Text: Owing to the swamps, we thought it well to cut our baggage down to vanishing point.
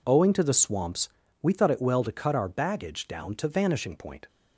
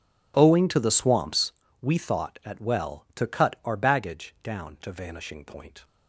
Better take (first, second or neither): first